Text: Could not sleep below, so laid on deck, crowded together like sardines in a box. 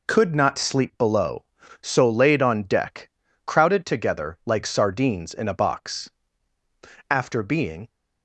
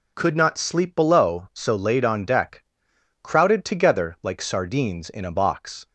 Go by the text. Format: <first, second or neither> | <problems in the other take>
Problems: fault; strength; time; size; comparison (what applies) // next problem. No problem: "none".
second | goes on to say "After being"; noticeable; from 7.0 s on; 0.78 s long